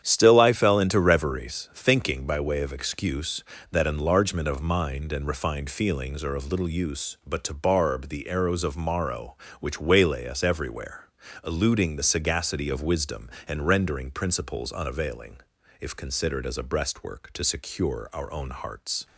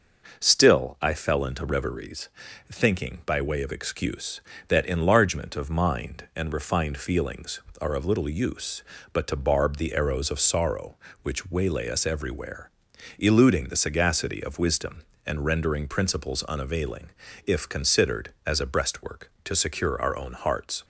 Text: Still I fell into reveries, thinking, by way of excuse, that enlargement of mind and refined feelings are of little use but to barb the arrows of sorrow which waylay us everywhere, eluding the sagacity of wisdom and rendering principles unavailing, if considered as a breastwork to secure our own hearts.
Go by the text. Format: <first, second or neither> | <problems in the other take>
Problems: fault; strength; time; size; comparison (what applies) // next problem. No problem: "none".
second | starts louder than the rest; strong; until 1.0 s; 9 dB // says "morrow" for "sorrow"; at 8.7 s